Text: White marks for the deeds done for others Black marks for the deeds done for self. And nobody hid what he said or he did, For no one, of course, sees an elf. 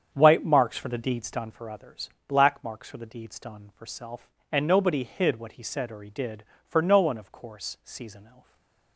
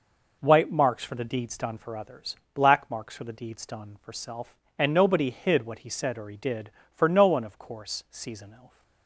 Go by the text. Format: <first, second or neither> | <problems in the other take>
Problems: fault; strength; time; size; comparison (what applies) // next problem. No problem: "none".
second | starts louder than the rest; strong; until 1.5 s; 8 dB // pauses between "others" and "Black"; slight; at 2.0 s; 0.16 s long; slight in the second // stays silent after the last word; slight; from 8.4 s on; 0.5 s long